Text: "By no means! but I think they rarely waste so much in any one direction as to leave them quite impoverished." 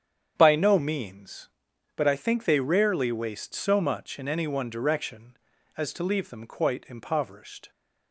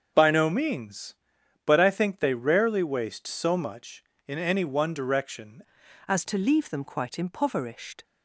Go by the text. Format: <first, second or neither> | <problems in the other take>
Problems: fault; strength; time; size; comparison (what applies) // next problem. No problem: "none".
first | starts louder than the rest; until 1.1 s; 7 dB; strong in the first // changes voice at "as"; from 6.0 s on; 2.0 s long